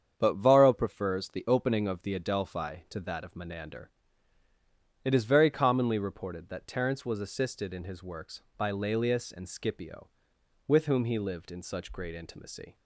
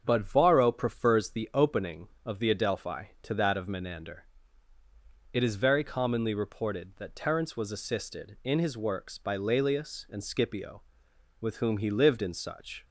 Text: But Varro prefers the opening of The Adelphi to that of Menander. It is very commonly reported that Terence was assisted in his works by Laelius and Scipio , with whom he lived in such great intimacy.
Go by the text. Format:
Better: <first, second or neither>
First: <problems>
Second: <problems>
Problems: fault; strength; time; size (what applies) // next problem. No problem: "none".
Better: first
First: starts louder than the rest; strong; until 1.1 s; 8 dB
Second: starts louder than the rest; strong; until 1.0 s; 7.5 dB // stops before "great intimacy"; at 12.8 s